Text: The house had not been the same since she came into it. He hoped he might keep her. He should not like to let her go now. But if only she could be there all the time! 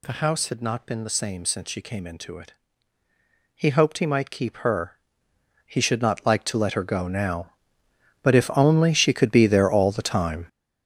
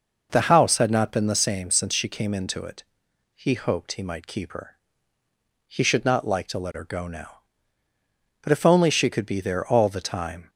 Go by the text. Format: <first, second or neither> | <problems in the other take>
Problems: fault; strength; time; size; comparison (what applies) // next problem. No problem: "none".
second | gets louder; strong; throughout; 10 dB